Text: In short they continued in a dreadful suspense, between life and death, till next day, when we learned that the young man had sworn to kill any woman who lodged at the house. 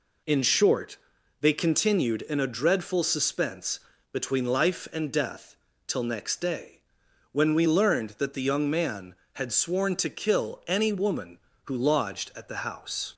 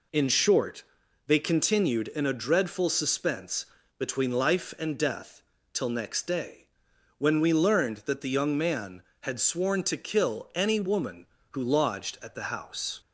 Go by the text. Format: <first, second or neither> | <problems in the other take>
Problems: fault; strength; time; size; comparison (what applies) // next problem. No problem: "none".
neither | pauses between "short" and "they"; the same in both